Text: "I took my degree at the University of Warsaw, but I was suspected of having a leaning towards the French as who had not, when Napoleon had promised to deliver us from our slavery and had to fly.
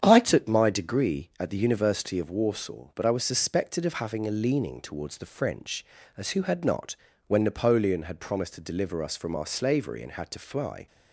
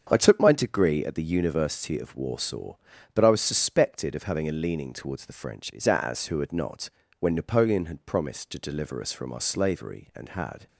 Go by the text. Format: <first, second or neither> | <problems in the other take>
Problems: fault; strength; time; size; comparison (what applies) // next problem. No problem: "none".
first | starts louder than the rest; strong; until 1.1 s; 7 dB; strong in the first // stops before "to fly"; at 10.6 s